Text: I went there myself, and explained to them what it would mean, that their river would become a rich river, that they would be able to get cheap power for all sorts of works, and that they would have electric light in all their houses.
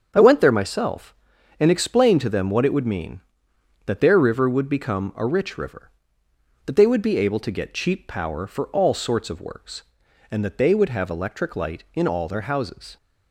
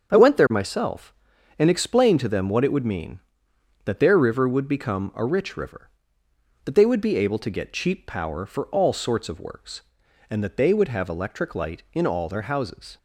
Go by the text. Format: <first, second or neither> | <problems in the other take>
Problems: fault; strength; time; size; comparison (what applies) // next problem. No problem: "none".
neither | starts louder than the rest; the same in both